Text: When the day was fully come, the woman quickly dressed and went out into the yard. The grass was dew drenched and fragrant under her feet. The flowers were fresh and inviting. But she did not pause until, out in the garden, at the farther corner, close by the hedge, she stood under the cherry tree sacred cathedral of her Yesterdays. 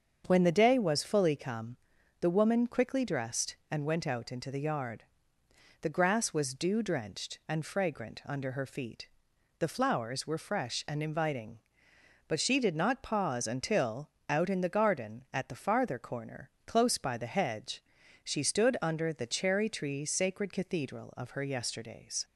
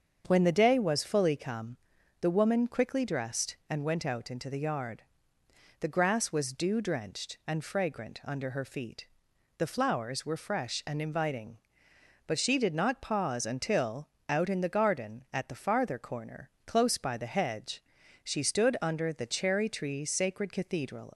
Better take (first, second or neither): first